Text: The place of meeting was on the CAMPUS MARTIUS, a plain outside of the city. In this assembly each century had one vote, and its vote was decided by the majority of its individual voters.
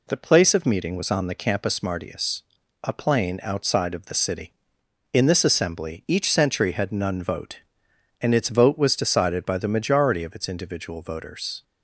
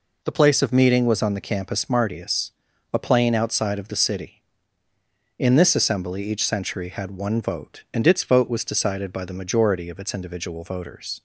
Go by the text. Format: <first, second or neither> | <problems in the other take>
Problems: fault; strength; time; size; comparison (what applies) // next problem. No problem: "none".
second | says "none" for "one"; at 6.9 s